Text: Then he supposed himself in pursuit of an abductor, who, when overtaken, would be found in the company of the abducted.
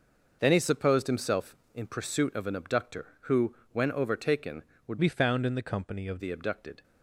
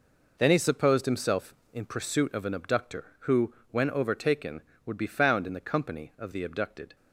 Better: second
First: changes voice from "be" to "of"; from 4.9 to 6.1 s; 1.2 s long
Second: none

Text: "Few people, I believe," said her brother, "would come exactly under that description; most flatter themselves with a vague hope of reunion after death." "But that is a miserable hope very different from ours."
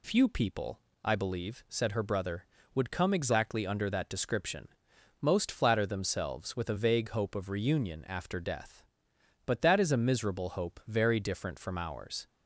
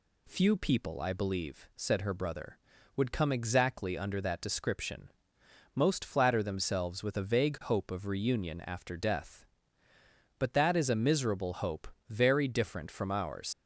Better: first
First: none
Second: pauses between "hope" and "very"; slight; at 11.8 s; 0.20 s long // leaves "ours" unfinished; at 13.5 s; 120 ms

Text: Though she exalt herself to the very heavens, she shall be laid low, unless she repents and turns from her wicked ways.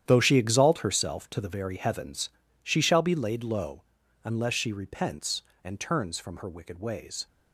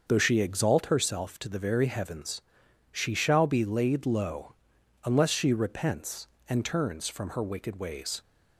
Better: second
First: gets quieter; strong; throughout; 13 dB // starts louder than the rest; strong; until 1.0 s; 10 dB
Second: starts louder than the rest; until 1.0 s; 6.5 dB

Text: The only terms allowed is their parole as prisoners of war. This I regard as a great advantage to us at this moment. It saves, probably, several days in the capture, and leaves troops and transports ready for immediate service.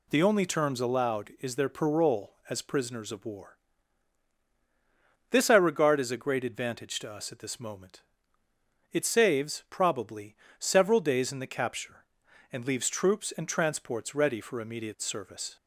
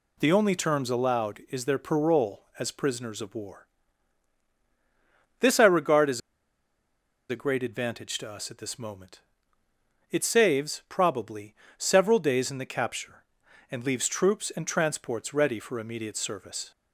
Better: first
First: none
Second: pauses between "as" and "a"; at 6.1 s; 1.0 s long

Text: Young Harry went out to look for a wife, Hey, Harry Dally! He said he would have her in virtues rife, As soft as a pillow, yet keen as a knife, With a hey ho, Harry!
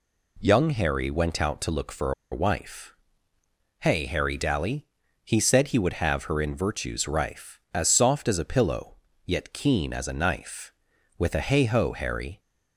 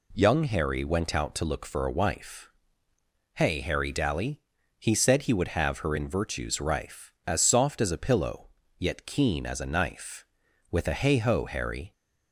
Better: second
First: pauses between "for" and "a"; slight; at 2.1 s; 0.20 s long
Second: none

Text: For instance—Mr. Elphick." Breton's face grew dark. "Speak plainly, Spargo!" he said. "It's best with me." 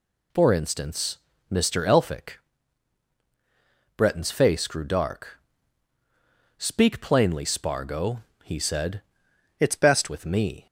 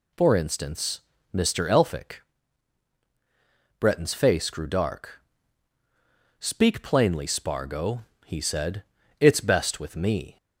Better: second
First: changes voice from "It's" to "best"; from 9.6 to 10.0 s; 0.4 s long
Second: none

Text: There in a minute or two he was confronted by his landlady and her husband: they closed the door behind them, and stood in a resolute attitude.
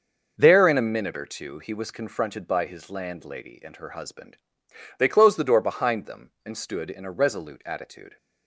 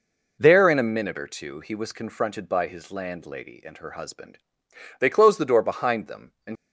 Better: first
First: none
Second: stops before "stood in a resolute attitude"; at 6.5 s

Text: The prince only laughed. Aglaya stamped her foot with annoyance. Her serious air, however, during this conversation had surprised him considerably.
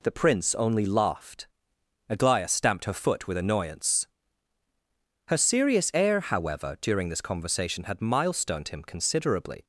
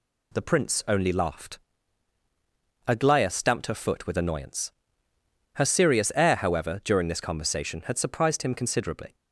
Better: second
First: says "milestoned" for "surprised"; at 8.0 s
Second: none

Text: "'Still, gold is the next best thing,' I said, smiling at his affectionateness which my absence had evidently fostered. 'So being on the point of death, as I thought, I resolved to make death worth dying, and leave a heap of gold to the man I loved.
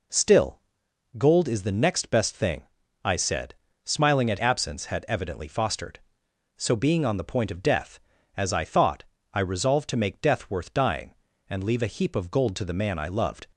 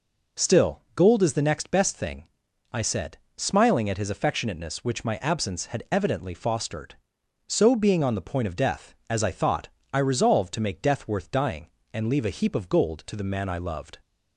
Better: second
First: skips "his affectionateness which my"; at 4.3 s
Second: none

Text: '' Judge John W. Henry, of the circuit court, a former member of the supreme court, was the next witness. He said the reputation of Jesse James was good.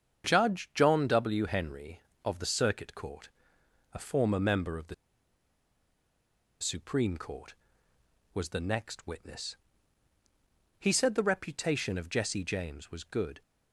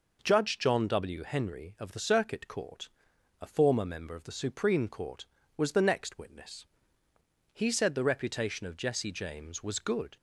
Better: second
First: starts louder than the rest; strong; until 1.3 s; 7.5 dB // pauses between "the" and "supreme"; strong; at 4.9 s; 1.6 s long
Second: none

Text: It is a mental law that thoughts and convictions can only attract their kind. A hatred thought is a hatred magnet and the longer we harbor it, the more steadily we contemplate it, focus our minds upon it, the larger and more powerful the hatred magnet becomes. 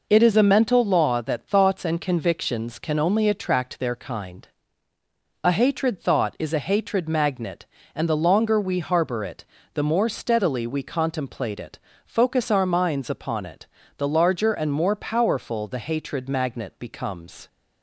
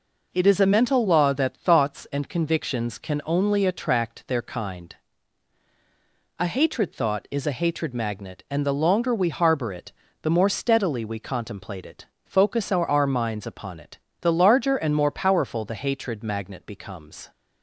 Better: first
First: none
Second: says "our" twice; at 12.8 s

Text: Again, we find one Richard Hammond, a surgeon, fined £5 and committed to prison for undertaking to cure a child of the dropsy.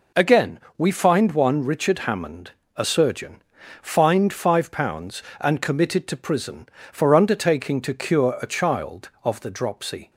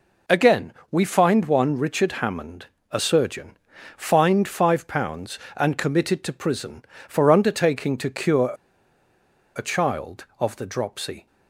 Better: first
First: none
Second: pauses between "cure" and "a"; at 8.5 s; 1.0 s long

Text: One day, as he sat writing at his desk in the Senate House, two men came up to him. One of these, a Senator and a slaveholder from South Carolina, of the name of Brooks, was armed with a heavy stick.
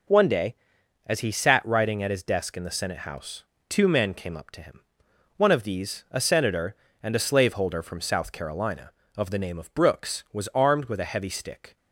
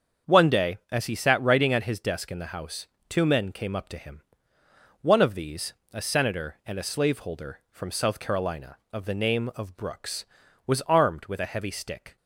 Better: first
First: none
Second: starts louder than the rest; strong; until 1.3 s; 7 dB // skips "Senate"; at 2.5 s

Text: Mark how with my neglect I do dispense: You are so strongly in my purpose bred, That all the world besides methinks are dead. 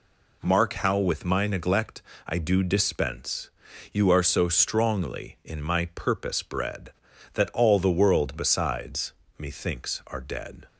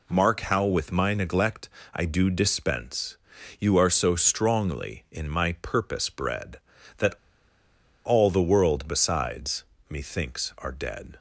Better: first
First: pauses between "neglect" and "I"; slight; at 2.0 s; 0.24 s long // pauses between "besides" and "methinks"; slight; at 9.1 s; 0.26 s long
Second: pauses between "neglect" and "I"; slight; at 1.6 s; 0.24 s long // pauses between "That" and "all"; noticeable; at 7.1 s; 0.89 s long // pauses between "besides" and "methinks"; slight; at 9.6 s; 0.26 s long

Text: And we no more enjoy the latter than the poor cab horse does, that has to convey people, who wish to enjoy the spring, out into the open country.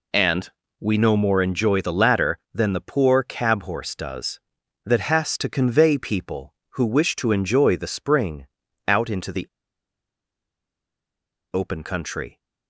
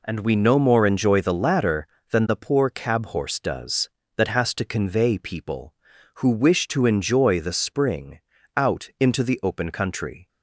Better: second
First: pauses between "And" and "we"; slight; at 0.4 s; 0.30 s long // pauses between "the" and "open"; strong; at 9.4 s; 2.0 s long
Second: none

